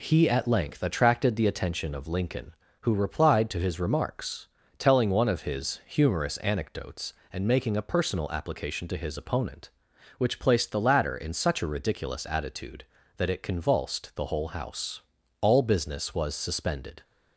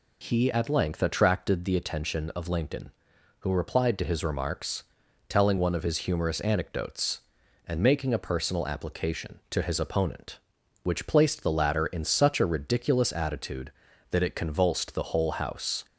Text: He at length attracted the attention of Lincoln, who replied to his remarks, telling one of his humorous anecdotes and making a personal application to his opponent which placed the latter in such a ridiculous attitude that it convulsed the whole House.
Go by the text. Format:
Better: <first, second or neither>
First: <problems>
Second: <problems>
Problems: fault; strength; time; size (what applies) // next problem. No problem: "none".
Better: second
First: goes on to say "All business was suspended"; from 15.4 s on; 1.6 s long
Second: none